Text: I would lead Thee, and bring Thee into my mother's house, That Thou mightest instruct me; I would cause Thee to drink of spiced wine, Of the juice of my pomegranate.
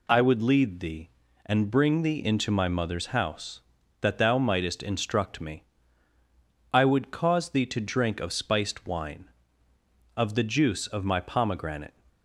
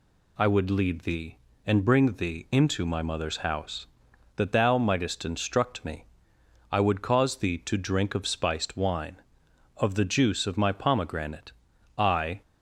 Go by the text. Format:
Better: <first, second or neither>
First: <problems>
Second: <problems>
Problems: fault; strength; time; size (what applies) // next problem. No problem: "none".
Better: first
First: none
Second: goes on to say "I"; slight; from 11.9 s on; 0.46 s long